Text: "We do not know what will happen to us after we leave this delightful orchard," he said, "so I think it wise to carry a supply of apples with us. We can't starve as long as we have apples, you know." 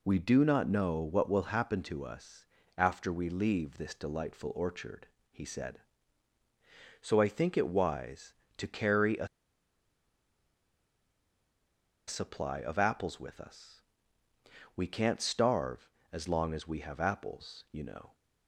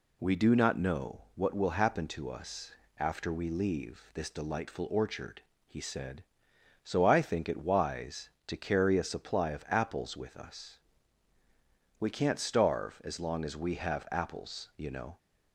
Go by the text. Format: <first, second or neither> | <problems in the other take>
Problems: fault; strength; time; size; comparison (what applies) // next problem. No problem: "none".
second | pauses between "us" and "after"; slight; at 2.4 s; 0.32 s long; slight in the second // pauses between "a" and "supply"; strong; at 9.2 s; 2.8 s long